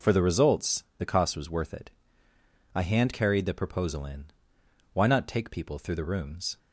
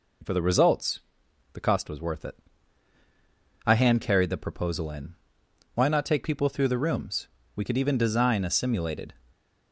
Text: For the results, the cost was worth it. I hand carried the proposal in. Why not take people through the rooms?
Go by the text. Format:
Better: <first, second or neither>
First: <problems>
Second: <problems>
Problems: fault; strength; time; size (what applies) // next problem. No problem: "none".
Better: first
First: none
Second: goes on to say "We could even design a simulated"; from 7.5 s on; 1.5 s long